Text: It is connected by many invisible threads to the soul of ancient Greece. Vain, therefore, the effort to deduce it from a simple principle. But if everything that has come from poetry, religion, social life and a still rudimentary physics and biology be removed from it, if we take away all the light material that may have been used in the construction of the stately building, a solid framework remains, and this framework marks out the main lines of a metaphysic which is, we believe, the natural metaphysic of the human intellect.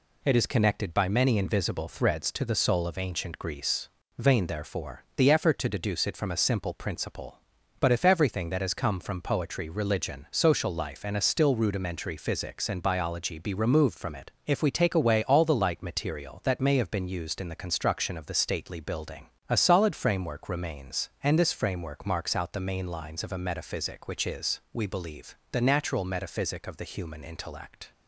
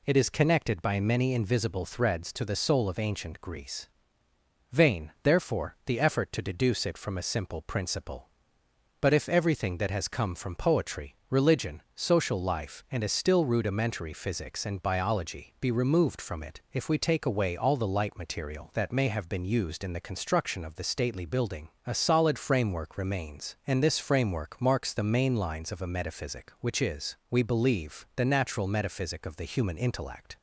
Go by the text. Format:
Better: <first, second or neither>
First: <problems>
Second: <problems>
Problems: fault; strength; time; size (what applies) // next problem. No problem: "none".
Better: first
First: none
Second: skips "out"; at 24.9 s